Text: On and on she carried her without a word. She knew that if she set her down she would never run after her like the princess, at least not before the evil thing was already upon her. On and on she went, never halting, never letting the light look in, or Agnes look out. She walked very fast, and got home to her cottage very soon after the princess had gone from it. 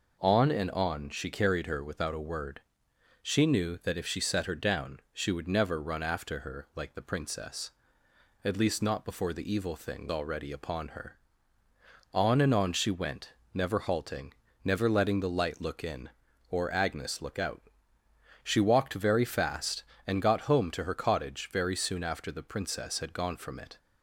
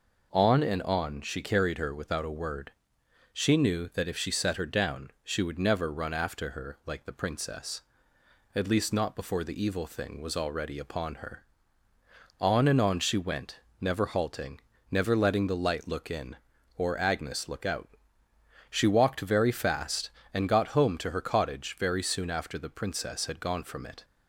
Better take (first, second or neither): second